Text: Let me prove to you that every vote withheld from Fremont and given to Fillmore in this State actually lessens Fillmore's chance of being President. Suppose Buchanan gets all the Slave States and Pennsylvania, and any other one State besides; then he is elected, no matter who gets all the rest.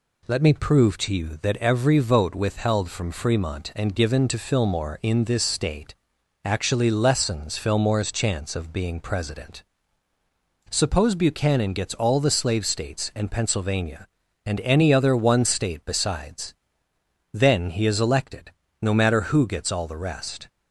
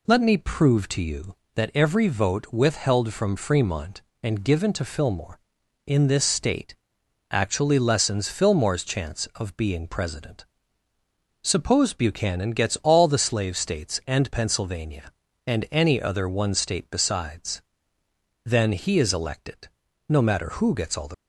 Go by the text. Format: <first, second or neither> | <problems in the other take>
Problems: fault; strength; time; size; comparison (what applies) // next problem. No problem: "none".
first | pauses between "State" and "actually"; noticeable; at 6.7 s; 0.56 s long; noticeable in the first // stops before "rest"; at 21.1 s